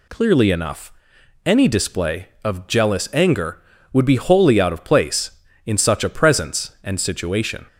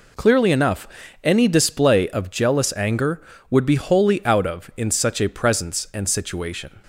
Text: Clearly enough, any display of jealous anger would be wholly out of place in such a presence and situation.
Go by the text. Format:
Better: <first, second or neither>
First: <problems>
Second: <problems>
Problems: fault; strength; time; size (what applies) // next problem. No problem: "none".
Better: first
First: none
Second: skips "place"; at 4.7 s